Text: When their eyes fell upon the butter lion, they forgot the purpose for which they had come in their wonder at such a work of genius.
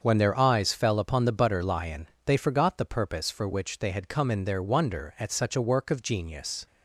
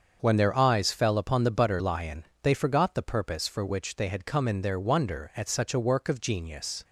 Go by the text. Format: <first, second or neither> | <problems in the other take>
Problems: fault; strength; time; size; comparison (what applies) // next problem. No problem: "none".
neither | starts louder than the rest; the same in both